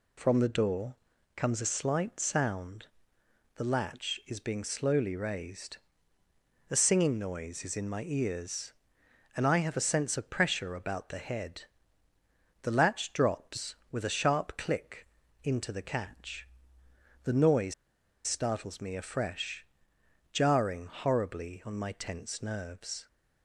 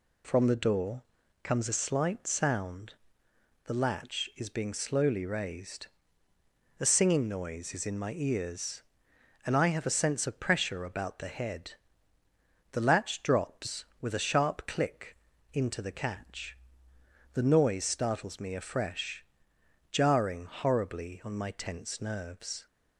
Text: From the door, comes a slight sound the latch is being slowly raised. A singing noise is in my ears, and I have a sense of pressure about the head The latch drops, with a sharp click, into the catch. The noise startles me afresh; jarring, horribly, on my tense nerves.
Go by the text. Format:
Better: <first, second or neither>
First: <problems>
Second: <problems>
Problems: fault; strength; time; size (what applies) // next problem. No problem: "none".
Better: second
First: pauses between "sound" and "the"; noticeable; at 2.8 s; 0.68 s long // pauses between "head" and "The"; at 11.6 s; 1.0 s long // pauses between "noise" and "startles"; noticeable; at 17.7 s; 0.53 s long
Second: pauses between "sound" and "the"; noticeable; at 2.9 s; 0.70 s long // pauses between "head" and "The"; at 11.7 s; 1.0 s long